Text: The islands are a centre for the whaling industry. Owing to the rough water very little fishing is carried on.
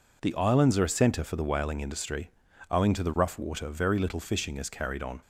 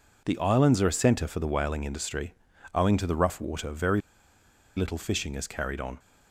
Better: first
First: none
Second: pauses between "very" and "little"; noticeable; at 4.0 s; 0.76 s long

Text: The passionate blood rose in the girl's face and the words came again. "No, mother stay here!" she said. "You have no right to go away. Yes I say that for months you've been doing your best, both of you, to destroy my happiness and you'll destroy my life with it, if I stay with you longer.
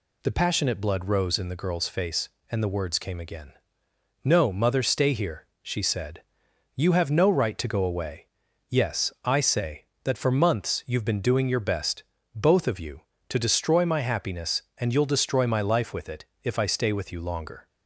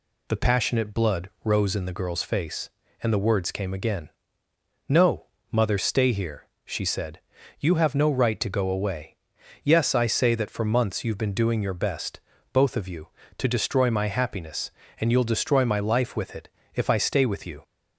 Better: first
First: none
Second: stops before "longer"; at 17.6 s

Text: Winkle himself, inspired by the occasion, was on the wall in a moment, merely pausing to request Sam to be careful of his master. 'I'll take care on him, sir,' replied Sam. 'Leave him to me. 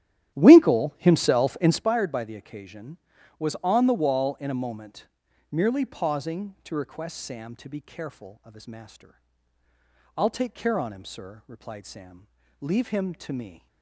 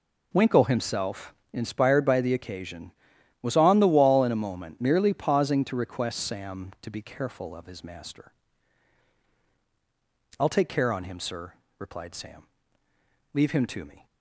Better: second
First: starts louder than the rest; strong; until 1.9 s; 12 dB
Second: none

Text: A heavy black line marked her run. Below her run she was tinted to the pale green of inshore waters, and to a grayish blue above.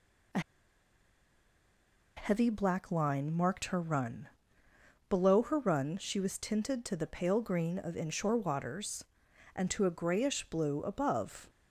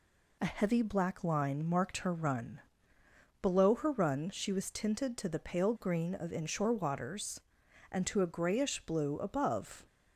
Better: second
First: pauses between "A" and "heavy"; strong; at 0.3 s; 1.7 s long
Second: none

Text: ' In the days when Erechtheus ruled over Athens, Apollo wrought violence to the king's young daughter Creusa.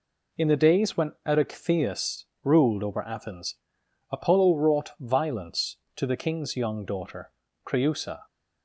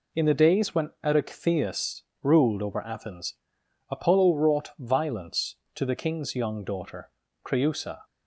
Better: neither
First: pauses between "Erechtheus" and "ruled"; slight; at 2.2 s; 0.16 s long // pauses between "daughter" and "Creusa"; slight; at 7.3 s; 0.34 s long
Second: pauses between "Erechtheus" and "ruled"; slight; at 2.0 s; 0.18 s long // pauses between "daughter" and "Creusa"; slight; at 7.1 s; 0.34 s long

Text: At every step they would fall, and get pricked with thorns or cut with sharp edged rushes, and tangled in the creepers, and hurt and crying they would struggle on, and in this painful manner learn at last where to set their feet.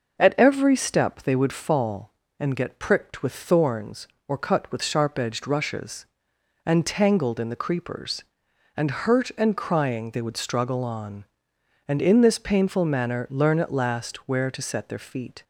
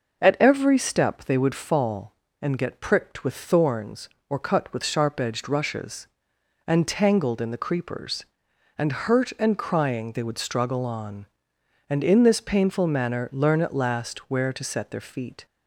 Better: neither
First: none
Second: none

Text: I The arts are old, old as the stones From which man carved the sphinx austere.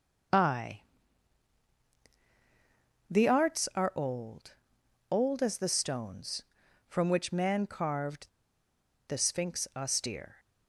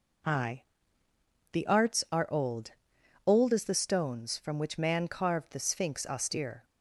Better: second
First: starts louder than the rest; until 3.6 s; 6 dB // pauses between "I" and "The"; strong; at 0.8 s; 2.2 s long // pauses between "carved" and "the"; noticeable; at 8.2 s; 0.80 s long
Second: pauses between "I" and "The"; noticeable; at 0.6 s; 0.92 s long

